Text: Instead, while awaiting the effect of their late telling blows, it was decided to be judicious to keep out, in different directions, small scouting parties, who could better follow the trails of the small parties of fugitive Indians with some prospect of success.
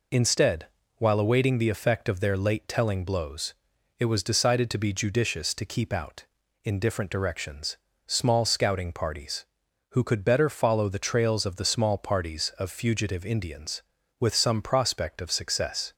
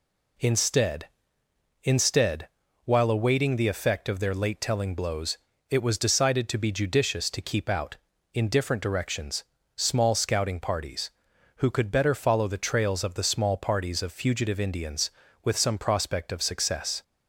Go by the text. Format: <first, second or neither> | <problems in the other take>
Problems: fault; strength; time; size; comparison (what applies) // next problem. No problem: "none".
first | says "Instead" twice; at 1.8 s